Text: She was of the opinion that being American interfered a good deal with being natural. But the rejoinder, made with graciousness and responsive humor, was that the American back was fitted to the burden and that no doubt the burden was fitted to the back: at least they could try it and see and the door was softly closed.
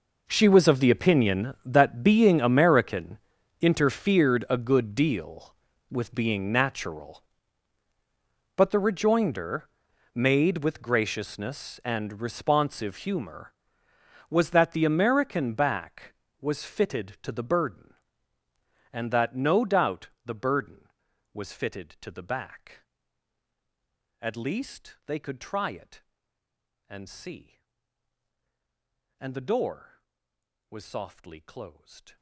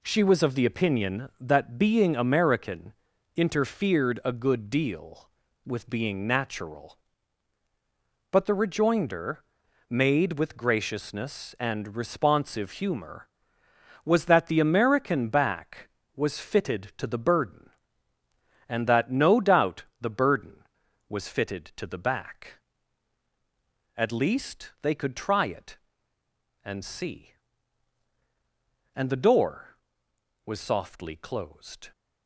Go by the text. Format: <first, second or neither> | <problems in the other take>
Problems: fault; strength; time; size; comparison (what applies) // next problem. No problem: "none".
second | gets quieter; strong; throughout; 19.5 dB // pauses between "American" and "interfered"; at 3.1 s; 0.44 s long; also in the second // pauses between "doubt" and "the"; slight; at 20.0 s; 0.16 s long; slight in the second